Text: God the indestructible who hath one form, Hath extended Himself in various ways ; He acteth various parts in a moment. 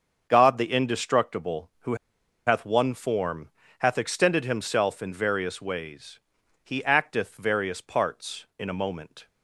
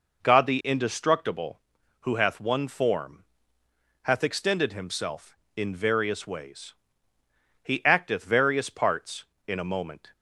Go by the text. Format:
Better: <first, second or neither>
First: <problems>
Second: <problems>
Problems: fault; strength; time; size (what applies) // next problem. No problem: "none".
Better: second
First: starts louder than the rest; until 1.3 s; 6.5 dB // pauses between "who" and "hath"; noticeable; at 1.9 s; 0.50 s long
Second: none